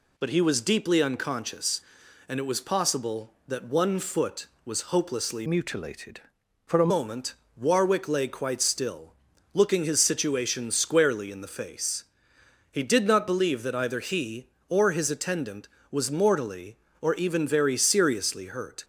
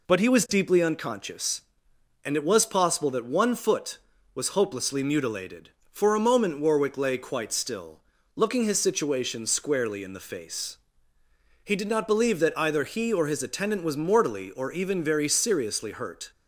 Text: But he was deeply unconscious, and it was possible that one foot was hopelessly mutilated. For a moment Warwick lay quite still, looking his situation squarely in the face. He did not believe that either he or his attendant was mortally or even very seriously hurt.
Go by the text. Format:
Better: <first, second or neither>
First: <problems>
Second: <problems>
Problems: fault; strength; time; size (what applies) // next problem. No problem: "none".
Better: second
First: changes voice from "mutilated" to "a"; from 5.4 to 6.9 s; 1.5 s long // pauses between "moment" and "Warwick"; slight; at 7.3 s; 0.22 s long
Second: none